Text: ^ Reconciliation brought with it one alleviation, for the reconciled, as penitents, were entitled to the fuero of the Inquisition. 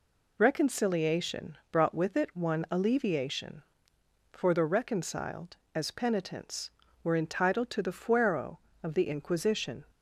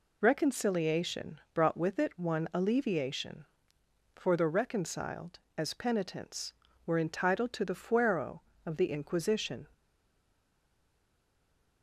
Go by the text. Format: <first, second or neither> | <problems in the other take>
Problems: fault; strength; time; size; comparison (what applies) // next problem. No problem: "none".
first | stays silent after the last word; noticeable; from 9.7 s on; 2.1 s long